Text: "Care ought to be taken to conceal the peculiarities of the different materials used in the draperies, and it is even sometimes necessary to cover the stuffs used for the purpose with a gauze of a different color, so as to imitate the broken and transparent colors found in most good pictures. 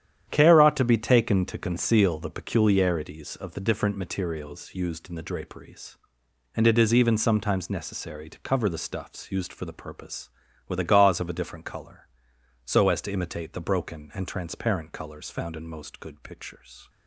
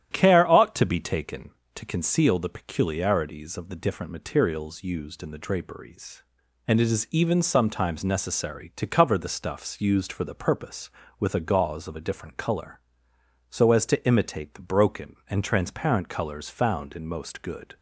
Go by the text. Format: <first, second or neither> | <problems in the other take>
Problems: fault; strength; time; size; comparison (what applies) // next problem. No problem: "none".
first | starts louder than the rest; strong; until 1.1 s; 11 dB; strong in the first // stops before "pictures"; at 17.7 s